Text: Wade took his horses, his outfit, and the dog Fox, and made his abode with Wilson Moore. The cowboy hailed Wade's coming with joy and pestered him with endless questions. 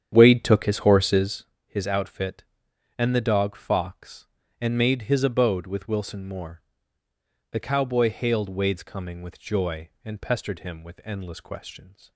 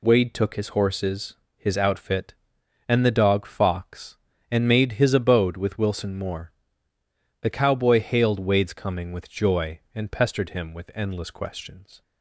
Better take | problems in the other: second | starts louder than the rest; strong; until 1.5 s; 9 dB

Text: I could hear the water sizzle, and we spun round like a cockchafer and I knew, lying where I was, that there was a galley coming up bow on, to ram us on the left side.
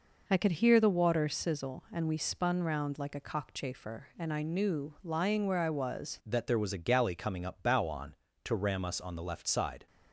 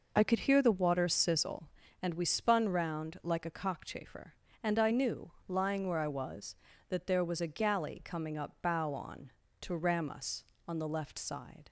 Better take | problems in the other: second | changes voice at "that"; from 6.2 s on; 3.6 s long

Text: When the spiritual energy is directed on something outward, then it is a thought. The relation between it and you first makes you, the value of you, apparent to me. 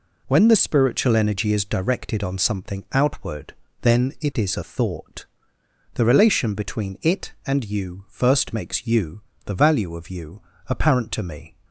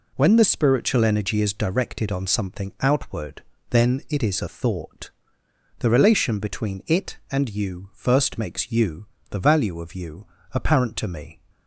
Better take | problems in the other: neither | none

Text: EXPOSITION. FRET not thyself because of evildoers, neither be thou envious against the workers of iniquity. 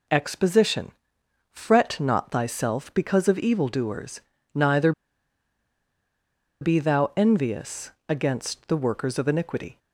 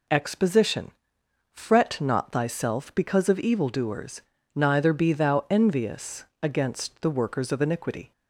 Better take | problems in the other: second | pauses between "neither" and "be"; strong; at 4.9 s; 1.7 s long // pauses between "envious" and "against"; slight; at 7.9 s; 0.18 s long; slight in the second

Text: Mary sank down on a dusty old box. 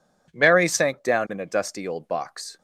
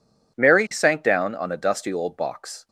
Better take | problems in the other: second | says "in" for "on"; at 1.3 s

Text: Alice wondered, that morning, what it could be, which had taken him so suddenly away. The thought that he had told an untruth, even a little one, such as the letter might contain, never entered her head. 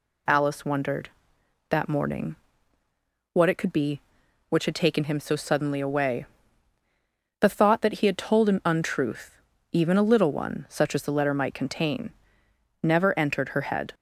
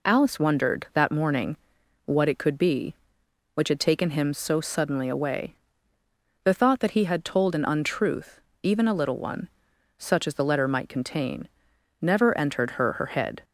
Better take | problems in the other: first | says "her" twice; at 12.9 s

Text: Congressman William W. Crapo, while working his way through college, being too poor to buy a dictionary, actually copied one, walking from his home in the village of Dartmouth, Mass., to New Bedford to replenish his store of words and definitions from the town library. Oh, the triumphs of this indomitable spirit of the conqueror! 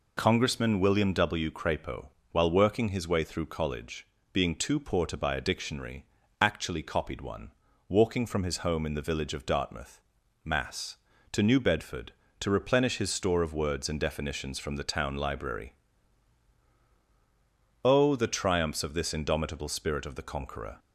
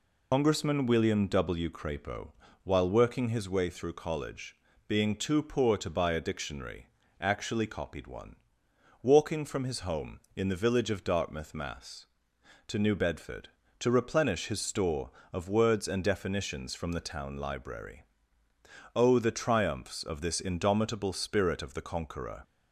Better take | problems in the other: first | loses the start of "Congressman"; at 0.3 s; 105 ms

